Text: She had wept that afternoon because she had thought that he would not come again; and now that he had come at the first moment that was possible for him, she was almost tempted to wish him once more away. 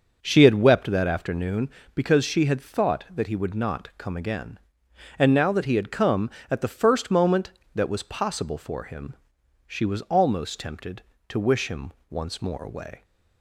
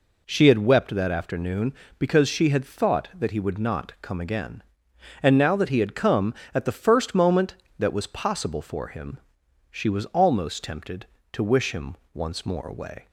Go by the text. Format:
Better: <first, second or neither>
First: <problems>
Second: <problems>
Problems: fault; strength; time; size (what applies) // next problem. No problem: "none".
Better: second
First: starts louder than the rest; noticeable; until 1.6 s; 6 dB // pauses between "him" and "once"; slight; at 11.9 s; 0.18 s long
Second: pauses between "him" and "once"; slight; at 11.9 s; 0.18 s long